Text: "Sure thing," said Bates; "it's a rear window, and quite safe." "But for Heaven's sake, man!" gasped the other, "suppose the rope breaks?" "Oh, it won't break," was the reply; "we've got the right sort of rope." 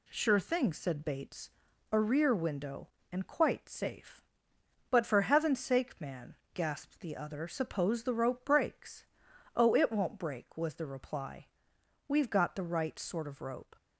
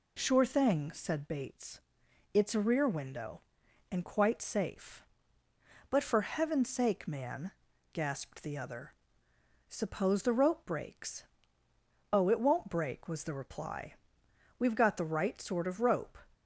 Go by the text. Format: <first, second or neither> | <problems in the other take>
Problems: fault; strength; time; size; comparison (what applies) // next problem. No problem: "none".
second | skips "it's"; at 1.7 s